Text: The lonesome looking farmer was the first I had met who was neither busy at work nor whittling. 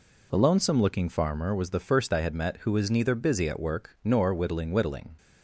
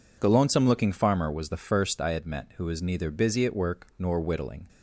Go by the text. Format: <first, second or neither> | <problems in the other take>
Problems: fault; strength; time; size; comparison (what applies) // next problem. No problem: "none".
second | says "whittling" twice; at 4.7 s